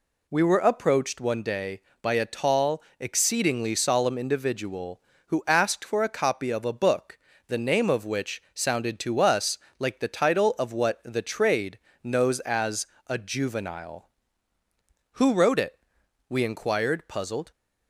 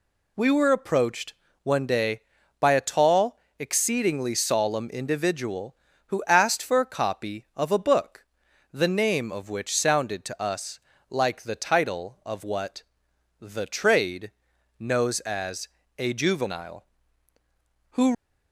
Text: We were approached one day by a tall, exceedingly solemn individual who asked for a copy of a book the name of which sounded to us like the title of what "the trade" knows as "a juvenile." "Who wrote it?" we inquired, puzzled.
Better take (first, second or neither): first